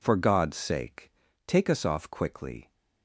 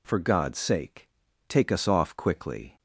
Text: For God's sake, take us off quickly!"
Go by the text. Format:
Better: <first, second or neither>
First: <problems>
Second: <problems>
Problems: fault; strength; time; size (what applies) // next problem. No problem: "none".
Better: neither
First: none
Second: none